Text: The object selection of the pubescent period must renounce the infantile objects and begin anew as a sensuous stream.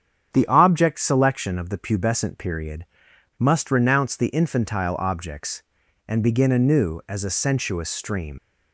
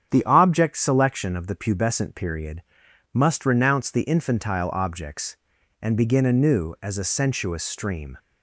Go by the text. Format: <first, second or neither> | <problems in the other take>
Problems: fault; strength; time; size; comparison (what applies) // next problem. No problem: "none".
second | starts louder than the rest; strong; until 1.3 s; 8 dB; strong in the second // pauses between "period" and "must"; noticeable; at 2.8 s; 0.52 s long; noticeable in the second // leaves "stream" unfinished; at 8.3 s; 60 ms